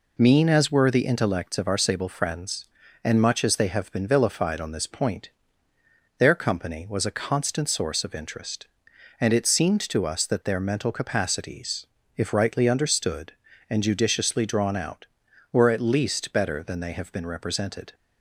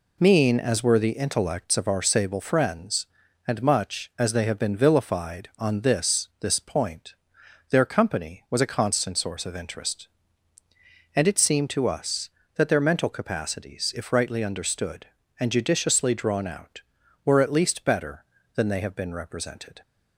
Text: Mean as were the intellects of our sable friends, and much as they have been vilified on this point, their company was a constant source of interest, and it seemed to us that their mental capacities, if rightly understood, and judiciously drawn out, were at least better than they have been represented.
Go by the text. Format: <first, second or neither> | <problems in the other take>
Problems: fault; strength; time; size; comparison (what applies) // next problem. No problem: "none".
first | says "this" twice; at 6.4 s